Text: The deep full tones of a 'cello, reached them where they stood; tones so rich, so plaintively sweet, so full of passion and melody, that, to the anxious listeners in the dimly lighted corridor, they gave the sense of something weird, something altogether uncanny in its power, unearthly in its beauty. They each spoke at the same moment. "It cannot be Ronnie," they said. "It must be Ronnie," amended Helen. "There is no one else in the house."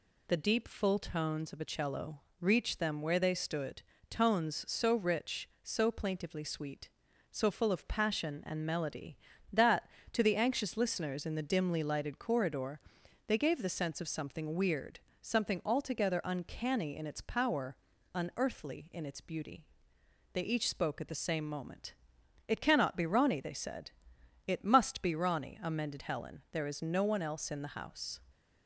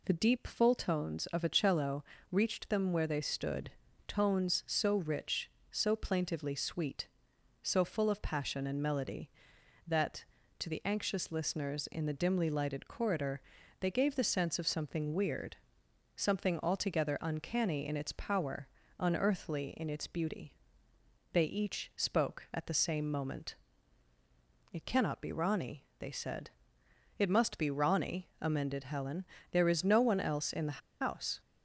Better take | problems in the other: first | pauses between "the" and "house"; slight; at 30.8 s; 0.22 s long

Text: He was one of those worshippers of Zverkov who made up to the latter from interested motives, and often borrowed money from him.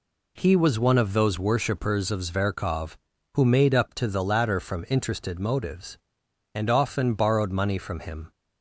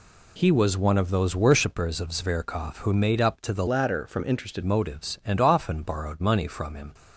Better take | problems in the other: first | changes voice from "latter" to "interested"; from 3.6 to 4.6 s; 1.0 s long

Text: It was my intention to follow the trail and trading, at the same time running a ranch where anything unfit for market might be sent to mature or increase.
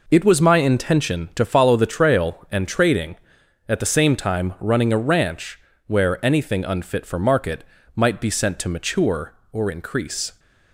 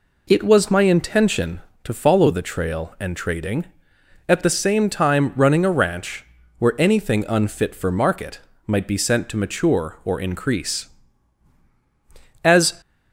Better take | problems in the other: first | pauses between "ranch" and "where"; slight; at 6.2 s; 0.32 s long; slight in the first // pauses between "market" and "might"; slight; at 8.3 s; 0.28 s long; slight in the first // goes on to say "As"; slight; from 12.4 s on; 0.36 s long

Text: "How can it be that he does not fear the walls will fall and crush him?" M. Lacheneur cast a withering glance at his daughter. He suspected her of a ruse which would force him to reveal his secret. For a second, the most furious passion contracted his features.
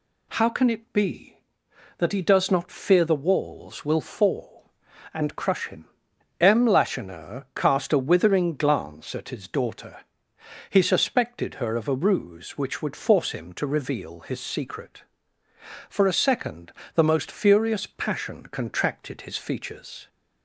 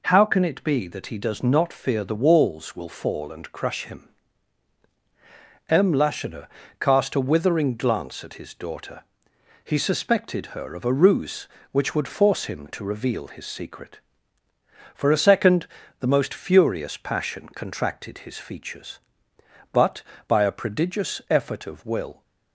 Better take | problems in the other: first | pauses between "Lacheneur" and "cast"; slight; at 6.4 s; 0.34 s long // goes on to say "But by a prodigious effort of will"; strong; from 19.7 s on; 2.5 s long

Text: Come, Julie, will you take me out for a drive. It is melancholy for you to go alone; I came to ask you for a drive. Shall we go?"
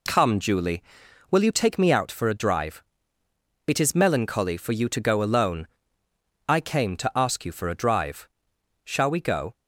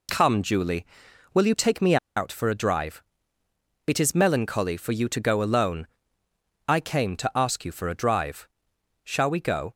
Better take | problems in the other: first | pauses between "me" and "out"; slight; at 1.9 s; 0.20 s long

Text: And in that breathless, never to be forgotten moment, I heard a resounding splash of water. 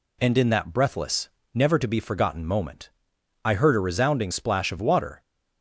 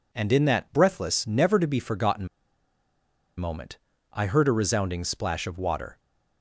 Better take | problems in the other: first | pauses between "forgotten" and "moment"; at 2.2 s; 1.0 s long

